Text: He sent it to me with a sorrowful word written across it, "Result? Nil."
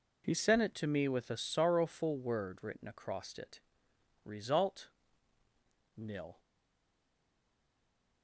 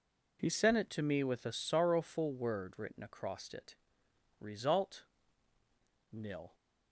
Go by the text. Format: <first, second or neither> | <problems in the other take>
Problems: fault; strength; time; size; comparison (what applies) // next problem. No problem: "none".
second | stays silent after the last word; noticeable; from 6.3 s on; 1.9 s long